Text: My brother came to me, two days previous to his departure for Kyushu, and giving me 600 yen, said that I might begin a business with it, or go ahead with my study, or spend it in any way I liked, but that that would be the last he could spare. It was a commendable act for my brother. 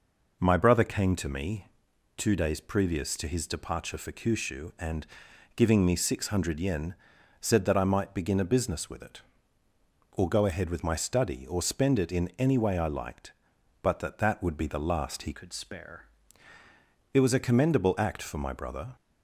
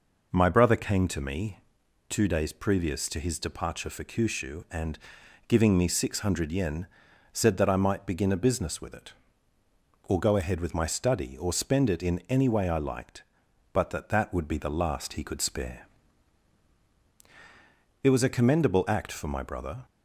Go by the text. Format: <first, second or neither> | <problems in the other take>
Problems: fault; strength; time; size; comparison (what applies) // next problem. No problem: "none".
second | pauses between "and" and "giving"; noticeable; at 5.0 s; 0.52 s long; noticeable in the second // changes voice from "could" to "spare"; from 15.3 to 16.0 s; 0.7 s long